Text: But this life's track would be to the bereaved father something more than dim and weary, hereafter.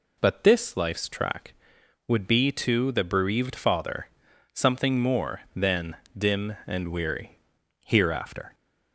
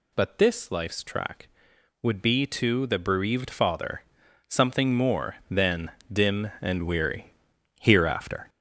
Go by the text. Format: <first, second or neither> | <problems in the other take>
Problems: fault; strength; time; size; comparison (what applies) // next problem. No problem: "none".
first | gets louder; noticeable; throughout; 5.5 dB // pauses between "father" and "something"; at 4.0 s; 0.44 s long; also in the first // pauses between "than" and "dim"; slight; at 5.9 s; 0.20 s long; slight in the first